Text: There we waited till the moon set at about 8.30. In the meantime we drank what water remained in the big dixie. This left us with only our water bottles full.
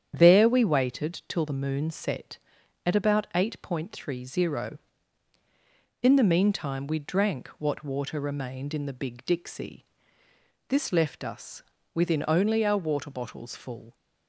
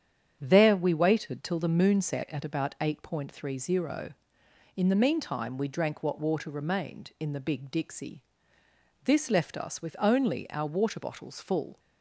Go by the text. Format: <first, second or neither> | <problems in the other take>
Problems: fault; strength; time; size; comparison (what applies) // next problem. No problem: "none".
second | starts louder than the rest; strong; until 1.1 s; 9 dB; strong in the second // says "within" for "with"; at 11.9 s